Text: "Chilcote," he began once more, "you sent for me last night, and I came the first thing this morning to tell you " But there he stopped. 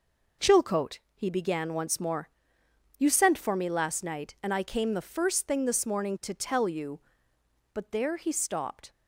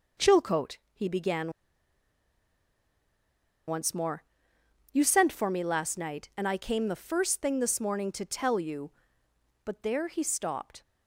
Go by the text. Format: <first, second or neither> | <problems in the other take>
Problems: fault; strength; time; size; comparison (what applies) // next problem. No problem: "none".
first | pauses between "began" and "once"; strong; at 1.5 s; 2.1 s long